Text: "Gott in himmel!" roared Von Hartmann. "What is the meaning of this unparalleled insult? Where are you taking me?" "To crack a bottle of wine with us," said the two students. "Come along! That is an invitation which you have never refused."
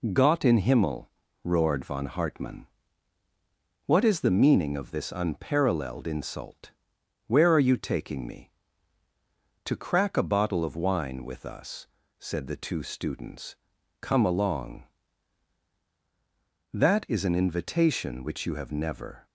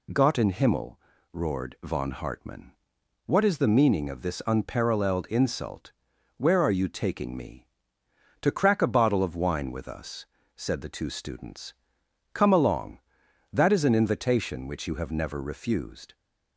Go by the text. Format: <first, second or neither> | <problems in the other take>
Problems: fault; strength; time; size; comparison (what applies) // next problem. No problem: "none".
second | stops before "refused"; at 19.2 s